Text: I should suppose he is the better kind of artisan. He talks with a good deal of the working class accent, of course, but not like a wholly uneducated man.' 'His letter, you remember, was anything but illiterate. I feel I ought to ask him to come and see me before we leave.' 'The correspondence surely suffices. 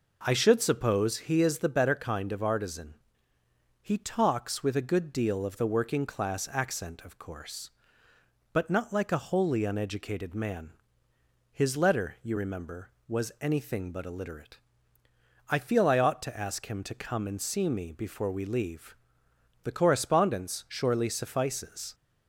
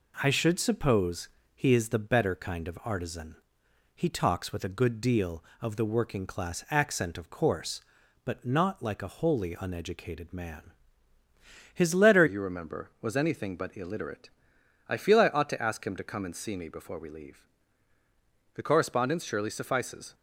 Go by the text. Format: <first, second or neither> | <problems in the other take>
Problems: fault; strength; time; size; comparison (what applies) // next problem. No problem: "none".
first | pauses between "suppose" and "he"; slight; at 1.2 s; 0.28 s long // changes voice at "you"; from 12.2 s on; 7.9 s long